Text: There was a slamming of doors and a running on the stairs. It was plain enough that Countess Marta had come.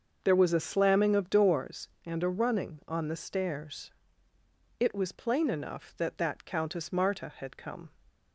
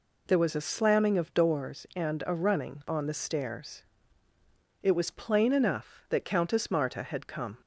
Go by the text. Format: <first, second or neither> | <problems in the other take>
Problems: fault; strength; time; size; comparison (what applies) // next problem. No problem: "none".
second | starts louder than the rest; until 1.2 s; 6.5 dB // says "that" twice; at 6.1 s